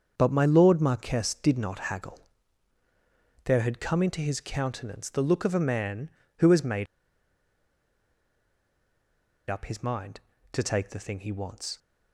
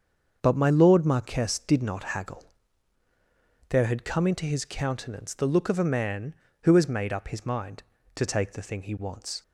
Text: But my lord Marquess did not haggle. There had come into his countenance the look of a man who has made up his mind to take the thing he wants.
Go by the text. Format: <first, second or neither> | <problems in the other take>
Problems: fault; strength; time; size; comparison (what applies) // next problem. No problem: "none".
second | starts louder than the rest; until 1.1 s; 6.5 dB; also in the second // pauses between "made" and "up"; strong; at 6.8 s; 2.6 s long